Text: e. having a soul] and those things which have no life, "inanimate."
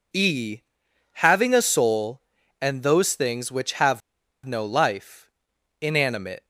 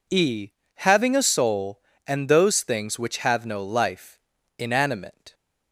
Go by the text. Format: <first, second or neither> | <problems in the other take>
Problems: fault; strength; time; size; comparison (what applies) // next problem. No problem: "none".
second | pauses between "have" and "no"; noticeable; at 4.0 s; 0.46 s long